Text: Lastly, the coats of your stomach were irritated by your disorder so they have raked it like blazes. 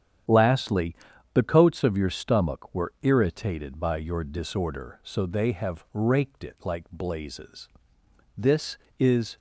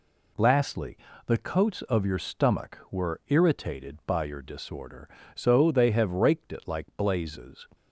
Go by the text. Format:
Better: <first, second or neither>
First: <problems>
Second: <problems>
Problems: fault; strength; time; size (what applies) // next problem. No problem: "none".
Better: second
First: starts louder than the rest; strong; until 1.6 s; 9 dB // goes on to say "This is"; noticeable; from 8.3 s on; 1.0 s long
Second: none